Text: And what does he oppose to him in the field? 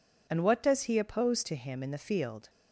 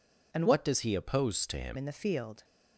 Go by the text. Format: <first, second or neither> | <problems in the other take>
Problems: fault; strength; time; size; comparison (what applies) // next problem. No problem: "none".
first | changes voice from "what" to "him"; from 0.4 to 1.7 s; 1.3 s long